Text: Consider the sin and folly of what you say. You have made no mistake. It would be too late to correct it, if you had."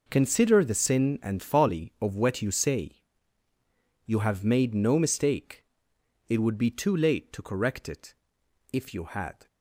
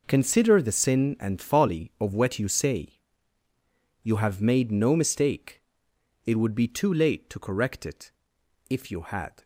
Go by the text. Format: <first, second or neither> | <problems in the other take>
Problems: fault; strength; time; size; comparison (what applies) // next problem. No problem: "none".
neither | none